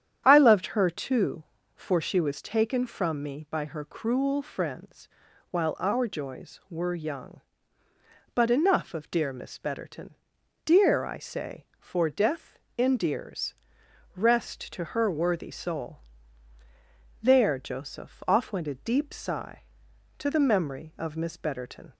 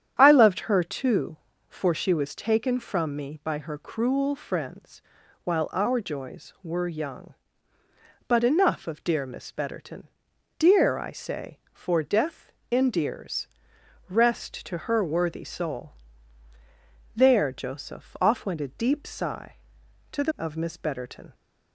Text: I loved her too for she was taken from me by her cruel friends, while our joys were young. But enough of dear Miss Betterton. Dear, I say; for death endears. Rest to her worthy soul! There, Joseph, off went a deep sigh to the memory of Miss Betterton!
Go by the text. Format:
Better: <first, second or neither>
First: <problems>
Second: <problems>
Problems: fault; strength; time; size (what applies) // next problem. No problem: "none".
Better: first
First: starts louder than the rest; strong; until 1.2 s; 9.5 dB // pauses between "death" and "endears"; slight; at 12.5 s; 0.20 s long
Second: starts louder than the rest; strong; until 1.1 s; 9.5 dB // pauses between "death" and "endears"; slight; at 12.5 s; 0.20 s long // skips "memory"; at 20.3 s